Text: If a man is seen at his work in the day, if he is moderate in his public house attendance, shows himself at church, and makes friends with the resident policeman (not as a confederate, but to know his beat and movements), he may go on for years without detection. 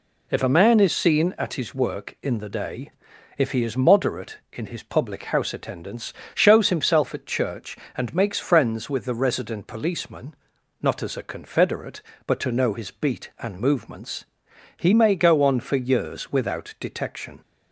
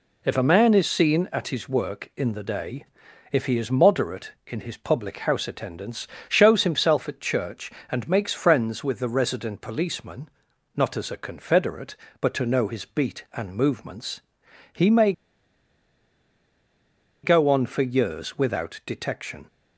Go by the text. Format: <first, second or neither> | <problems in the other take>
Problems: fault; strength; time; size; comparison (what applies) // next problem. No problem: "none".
first | pauses between "may" and "go"; strong; at 15.1 s; 2.1 s long